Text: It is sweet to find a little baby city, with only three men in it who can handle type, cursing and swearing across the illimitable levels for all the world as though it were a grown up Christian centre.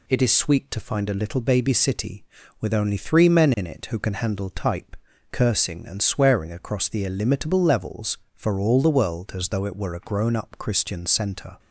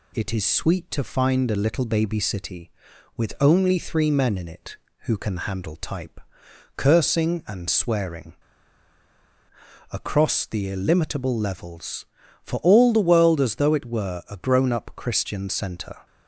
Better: first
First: none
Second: pauses between "swearing" and "across"; strong; at 8.3 s; 1.5 s long

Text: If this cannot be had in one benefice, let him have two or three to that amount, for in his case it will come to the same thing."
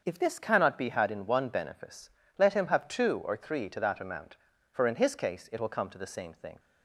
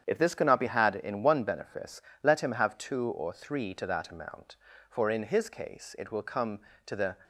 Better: first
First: starts louder than the rest; until 1.0 s; 7 dB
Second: starts louder than the rest; strong; until 1.0 s; 8.5 dB // stops before "same thing"; at 7.2 s

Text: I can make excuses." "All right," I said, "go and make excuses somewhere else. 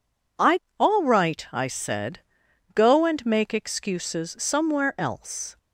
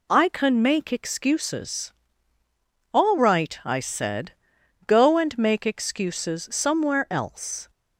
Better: second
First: skips "can make excuses"; at 0.6 s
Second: none

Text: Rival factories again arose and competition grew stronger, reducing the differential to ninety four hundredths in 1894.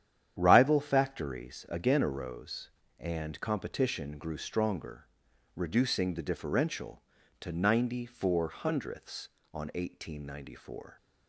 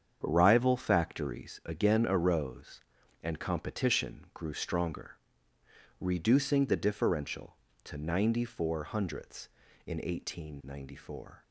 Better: second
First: starts louder than the rest; strong; until 1.3 s; 9.5 dB // says "on" for "in"; at 9.5 s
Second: starts louder than the rest; strong; until 1.2 s; 7.5 dB

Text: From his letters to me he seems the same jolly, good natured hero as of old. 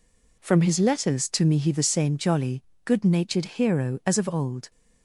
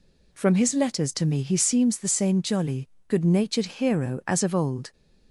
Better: second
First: skips "seems"; at 1.7 s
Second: none

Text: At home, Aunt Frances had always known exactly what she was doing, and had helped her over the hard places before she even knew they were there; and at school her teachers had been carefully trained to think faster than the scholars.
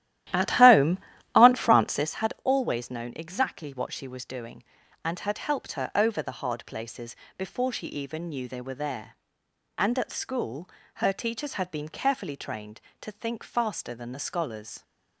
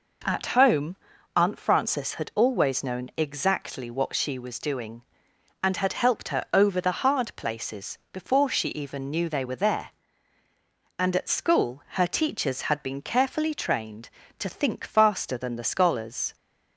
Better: second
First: starts louder than the rest; strong; until 2.1 s; 13 dB // pauses between "places" and "before"; slight; at 7.1 s; 0.22 s long // pauses between "school" and "her"; slight; at 10.6 s; 0.26 s long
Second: none

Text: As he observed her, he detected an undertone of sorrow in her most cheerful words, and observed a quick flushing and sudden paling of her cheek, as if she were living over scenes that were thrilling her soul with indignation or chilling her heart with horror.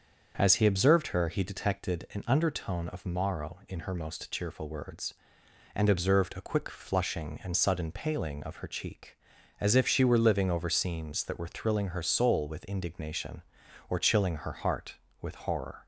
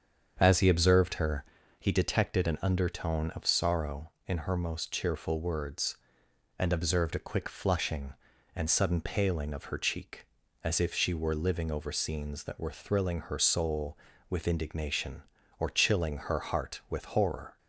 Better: second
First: starts louder than the rest; until 1.3 s; 7 dB // says "morrow" for "sorrow"; at 3.0 s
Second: starts louder than the rest; strong; until 1.4 s; 7 dB

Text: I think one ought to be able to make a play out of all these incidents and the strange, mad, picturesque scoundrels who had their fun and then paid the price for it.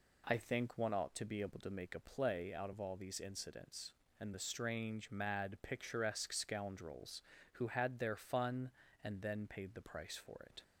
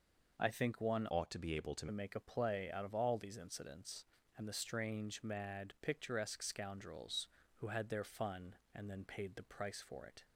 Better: first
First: none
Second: changes voice from "ought" to "to"; from 1.0 to 1.8 s; 0.8 s long

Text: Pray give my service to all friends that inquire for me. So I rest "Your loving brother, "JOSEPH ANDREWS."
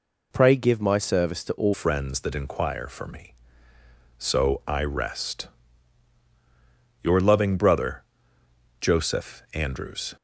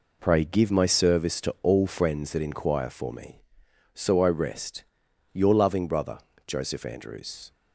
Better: second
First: changes voice at "friends"; from 1.7 s on; 8.4 s long // pauses between "rest" and "Your"; strong; at 5.4 s; 1.5 s long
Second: pauses between "rest" and "Your"; noticeable; at 4.8 s; 0.50 s long

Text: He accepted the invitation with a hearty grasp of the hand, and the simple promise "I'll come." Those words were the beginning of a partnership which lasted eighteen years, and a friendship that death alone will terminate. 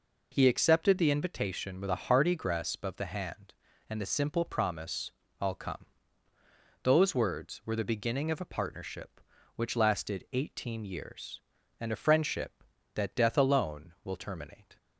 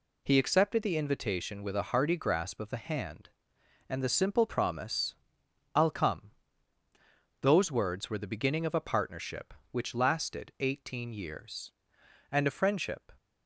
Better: first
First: pauses between "promise" and "I'll"; slight; at 5.1 s; 0.28 s long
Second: pauses between "promise" and "I'll"; noticeable; at 5.1 s; 0.60 s long // stops before "that death alone will terminate"; at 13.1 s

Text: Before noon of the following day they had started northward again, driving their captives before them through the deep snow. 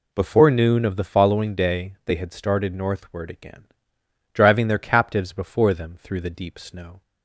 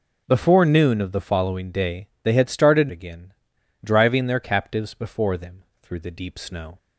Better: first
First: none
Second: skips "northward"; at 2.8 s // pauses between "them" and "through"; slight; at 5.6 s; 0.18 s long

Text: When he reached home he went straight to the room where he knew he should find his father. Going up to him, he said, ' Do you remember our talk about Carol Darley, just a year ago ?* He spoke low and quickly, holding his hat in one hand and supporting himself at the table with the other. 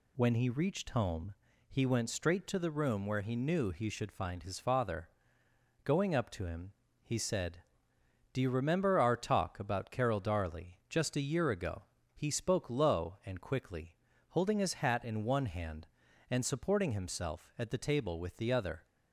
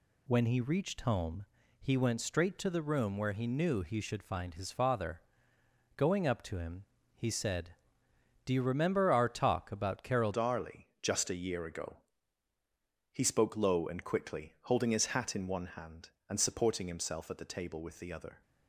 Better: first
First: pauses between "home" and "he"; slight; at 1.3 s; 0.34 s long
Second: pauses between "home" and "he"; slight; at 1.4 s; 0.34 s long // changes voice at "Darley"; from 10.3 s on; 8.1 s long

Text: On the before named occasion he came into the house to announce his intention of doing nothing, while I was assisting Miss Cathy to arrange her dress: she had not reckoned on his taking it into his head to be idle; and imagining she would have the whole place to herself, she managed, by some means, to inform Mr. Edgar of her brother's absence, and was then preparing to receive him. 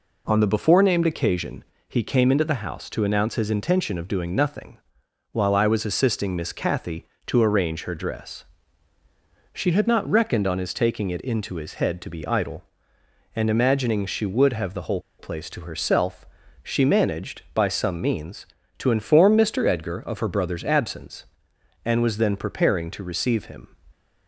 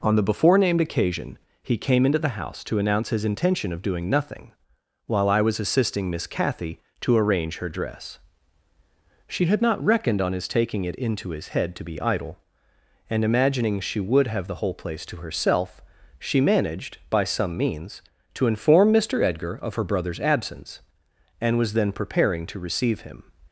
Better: second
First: pauses between "occasion" and "he"; slight; at 1.6 s; 0.26 s long // pauses between "whole" and "place"; slight; at 15.0 s; 0.18 s long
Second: pauses between "occasion" and "he"; slight; at 1.3 s; 0.26 s long

